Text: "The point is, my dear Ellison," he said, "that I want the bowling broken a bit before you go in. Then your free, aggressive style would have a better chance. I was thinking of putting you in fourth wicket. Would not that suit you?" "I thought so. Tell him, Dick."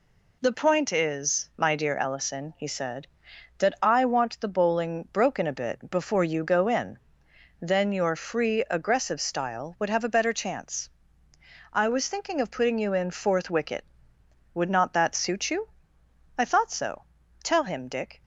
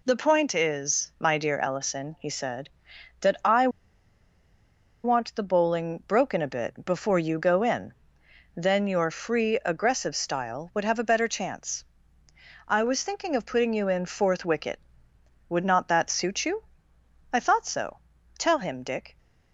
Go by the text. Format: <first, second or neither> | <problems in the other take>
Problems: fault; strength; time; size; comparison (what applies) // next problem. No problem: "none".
first | pauses between "I" and "want"; strong; at 3.6 s; 1.3 s long